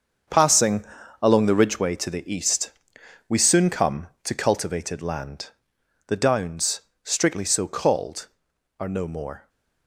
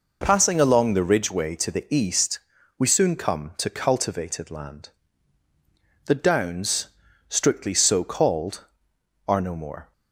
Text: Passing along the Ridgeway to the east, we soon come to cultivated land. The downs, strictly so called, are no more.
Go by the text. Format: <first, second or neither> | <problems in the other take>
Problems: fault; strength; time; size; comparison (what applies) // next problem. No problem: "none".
second | gets quieter; strong; throughout; 11 dB // pauses between "Passing" and "along"; at 0.8 s; 0.38 s long